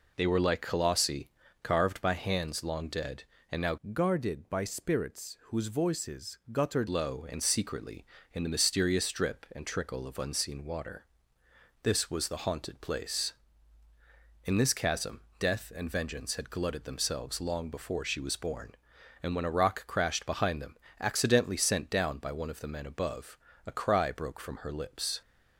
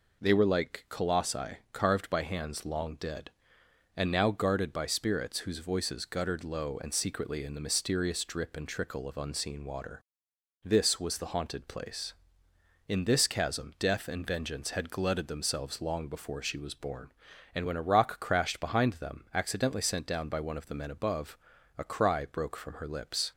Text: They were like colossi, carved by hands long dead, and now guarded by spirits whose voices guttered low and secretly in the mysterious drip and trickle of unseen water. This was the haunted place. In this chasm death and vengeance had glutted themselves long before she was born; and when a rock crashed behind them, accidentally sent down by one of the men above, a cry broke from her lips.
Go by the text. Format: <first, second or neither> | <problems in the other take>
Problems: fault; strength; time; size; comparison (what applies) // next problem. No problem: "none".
second | changes voice from "guarded" to "guttered"; from 3.9 to 6.8 s; 2.9 s long // pauses between "chasm" and "death"; slight; at 15.2 s; 0.18 s long